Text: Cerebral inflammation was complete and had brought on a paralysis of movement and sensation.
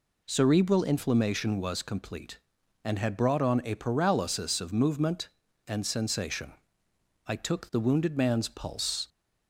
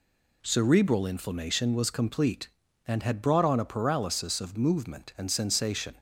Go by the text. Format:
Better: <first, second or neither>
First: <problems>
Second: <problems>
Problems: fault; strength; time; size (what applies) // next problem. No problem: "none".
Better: second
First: goes on to say "I took the wounded man's pulse"; strong; from 7.2 s on; 1.8 s long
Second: none